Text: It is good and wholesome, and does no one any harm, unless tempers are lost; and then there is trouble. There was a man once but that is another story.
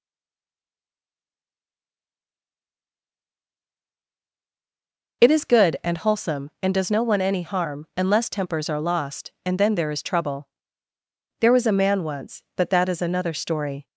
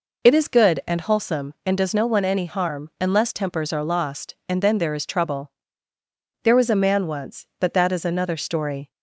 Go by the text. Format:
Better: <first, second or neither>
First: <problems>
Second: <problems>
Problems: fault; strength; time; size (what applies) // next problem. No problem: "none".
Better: second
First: stays silent before the first word; strong; until 5.2 s; 5.2 s long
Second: none